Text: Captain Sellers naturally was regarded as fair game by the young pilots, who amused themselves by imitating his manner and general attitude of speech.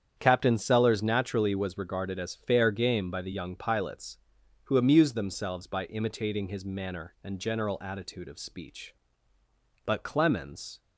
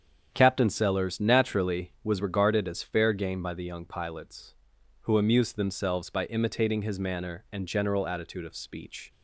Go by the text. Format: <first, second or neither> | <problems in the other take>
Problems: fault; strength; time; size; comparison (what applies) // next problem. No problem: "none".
second | starts louder than the rest; strong; until 1.1 s; 8.5 dB; strong in the second // goes on to say "But Clemens"; noticeable; from 9.8 s on; 0.96 s long